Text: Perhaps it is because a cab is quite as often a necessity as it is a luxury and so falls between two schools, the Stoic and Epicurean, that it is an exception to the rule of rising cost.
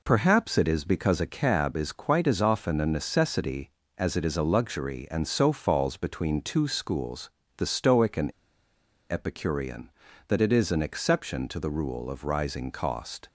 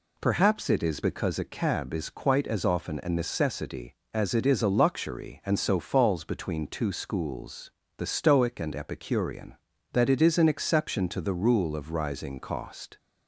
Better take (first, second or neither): second